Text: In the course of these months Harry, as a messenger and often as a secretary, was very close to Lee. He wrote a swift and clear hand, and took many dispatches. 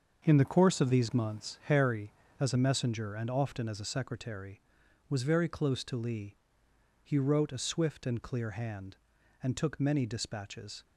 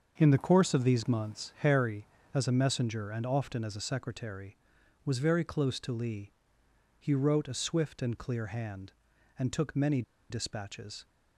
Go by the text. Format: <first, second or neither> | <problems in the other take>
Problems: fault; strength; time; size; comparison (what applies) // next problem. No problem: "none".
first | starts louder than the rest; until 1.1 s; 6.5 dB; also in the first // pauses between "many" and "dispatches"; slight; at 10.0 s; 0.28 s long